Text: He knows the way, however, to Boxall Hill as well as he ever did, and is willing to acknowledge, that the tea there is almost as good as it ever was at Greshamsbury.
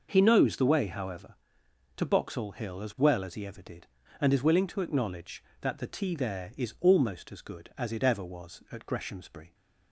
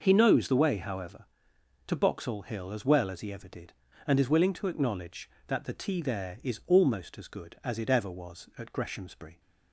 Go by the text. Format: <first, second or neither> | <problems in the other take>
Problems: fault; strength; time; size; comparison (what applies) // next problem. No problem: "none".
neither | none